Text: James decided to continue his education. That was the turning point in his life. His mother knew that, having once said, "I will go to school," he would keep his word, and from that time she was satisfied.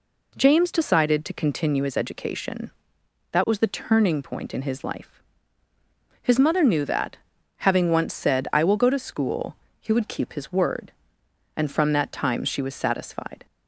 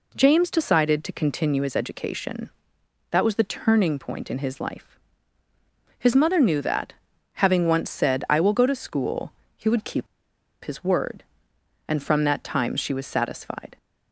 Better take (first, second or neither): first